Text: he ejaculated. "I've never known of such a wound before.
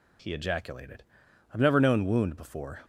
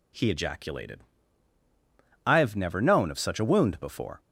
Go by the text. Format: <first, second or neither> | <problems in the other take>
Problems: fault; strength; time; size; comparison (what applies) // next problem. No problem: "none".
second | skips "of such a"; at 2.0 s